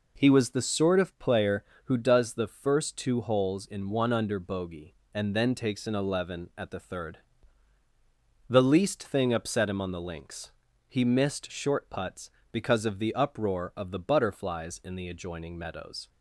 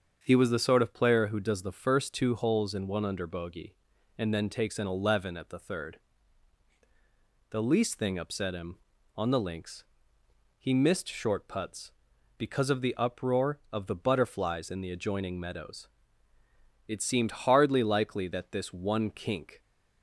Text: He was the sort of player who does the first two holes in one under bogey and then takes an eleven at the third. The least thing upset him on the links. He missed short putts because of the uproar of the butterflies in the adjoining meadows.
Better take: first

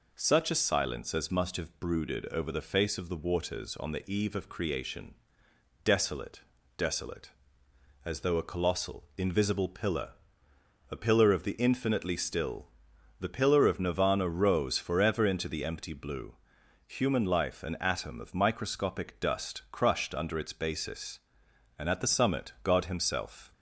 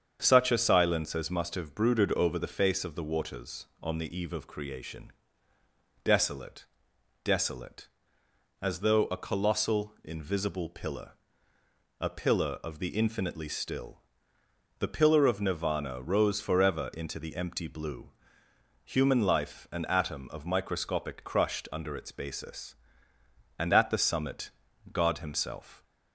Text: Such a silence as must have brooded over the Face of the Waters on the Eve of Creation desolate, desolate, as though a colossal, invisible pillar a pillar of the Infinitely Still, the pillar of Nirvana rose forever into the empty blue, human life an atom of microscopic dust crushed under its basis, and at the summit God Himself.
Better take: first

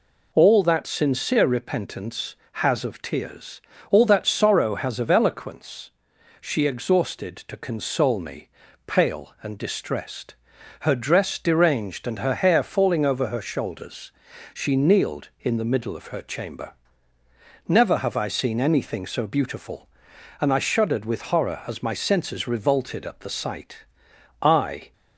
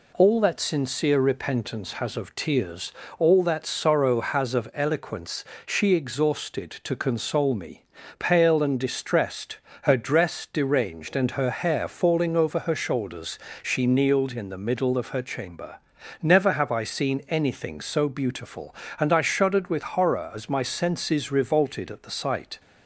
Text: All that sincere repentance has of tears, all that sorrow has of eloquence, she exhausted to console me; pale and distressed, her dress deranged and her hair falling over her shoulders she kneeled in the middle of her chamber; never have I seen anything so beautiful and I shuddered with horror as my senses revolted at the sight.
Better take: second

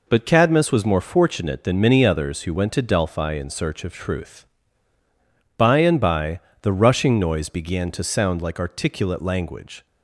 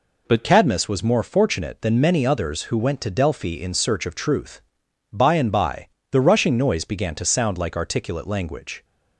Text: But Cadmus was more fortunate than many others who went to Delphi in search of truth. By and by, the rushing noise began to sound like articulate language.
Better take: first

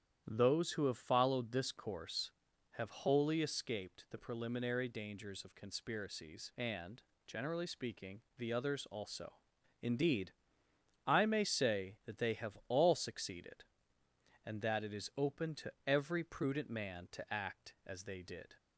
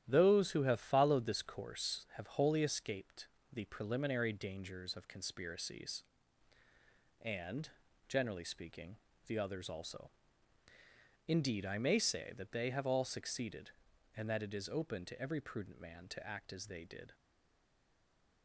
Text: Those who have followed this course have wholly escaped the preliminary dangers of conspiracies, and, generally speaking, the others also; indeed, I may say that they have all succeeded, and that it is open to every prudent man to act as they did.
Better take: first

